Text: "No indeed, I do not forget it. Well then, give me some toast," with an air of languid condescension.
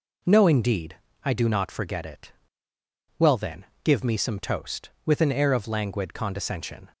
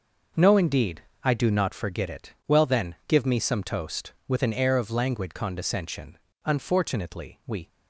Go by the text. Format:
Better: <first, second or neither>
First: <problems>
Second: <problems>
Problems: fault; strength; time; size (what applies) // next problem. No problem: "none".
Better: first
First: none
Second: goes on to say "Unfortunately we"; noticeable; from 6.4 s on; 1.2 s long